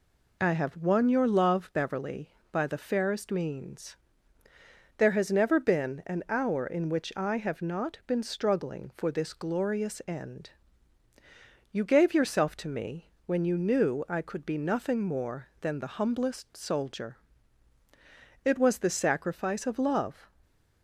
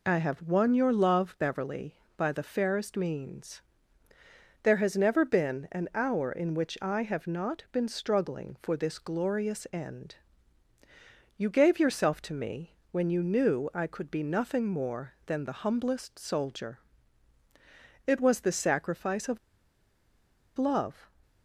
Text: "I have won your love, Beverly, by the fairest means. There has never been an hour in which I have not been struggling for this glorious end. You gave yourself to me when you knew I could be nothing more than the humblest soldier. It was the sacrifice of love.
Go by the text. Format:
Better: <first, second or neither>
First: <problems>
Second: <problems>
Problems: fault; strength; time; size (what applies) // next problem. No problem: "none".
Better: first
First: pauses between "me" and "when"; slight; at 13.1 s; 0.16 s long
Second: pauses between "me" and "when"; slight; at 12.7 s; 0.16 s long // pauses between "of" and "love"; at 19.3 s; 1.1 s long